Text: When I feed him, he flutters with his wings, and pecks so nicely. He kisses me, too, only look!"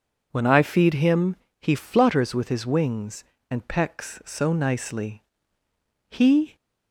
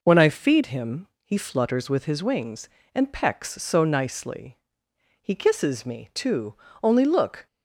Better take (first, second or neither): second